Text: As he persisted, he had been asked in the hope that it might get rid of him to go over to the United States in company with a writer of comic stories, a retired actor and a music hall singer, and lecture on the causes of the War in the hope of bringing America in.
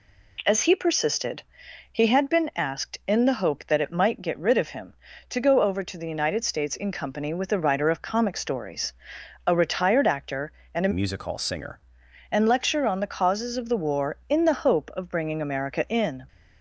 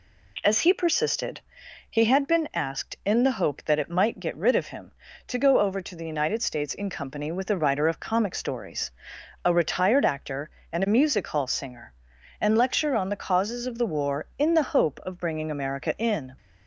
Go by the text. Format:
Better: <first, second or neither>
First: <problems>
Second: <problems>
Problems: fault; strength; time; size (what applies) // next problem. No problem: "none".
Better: second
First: changes voice from "music" to "singer"; from 10.9 to 11.7 s; 0.8 s long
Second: none